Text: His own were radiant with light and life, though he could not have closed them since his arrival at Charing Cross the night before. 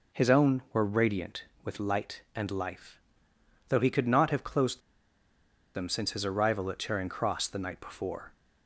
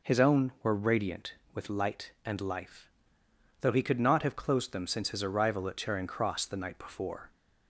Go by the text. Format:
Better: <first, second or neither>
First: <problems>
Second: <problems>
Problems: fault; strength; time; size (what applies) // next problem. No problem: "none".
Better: second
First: pauses between "closed" and "them"; noticeable; at 4.8 s; 0.94 s long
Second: none